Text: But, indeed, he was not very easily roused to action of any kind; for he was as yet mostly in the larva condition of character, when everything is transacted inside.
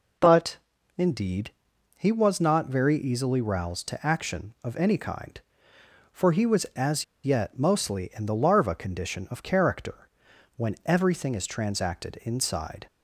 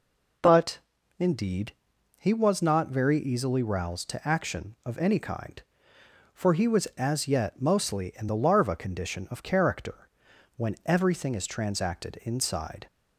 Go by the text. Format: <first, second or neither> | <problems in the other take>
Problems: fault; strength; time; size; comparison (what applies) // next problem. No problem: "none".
second | pauses between "as" and "yet"; slight; at 7.0 s; 0.19 s long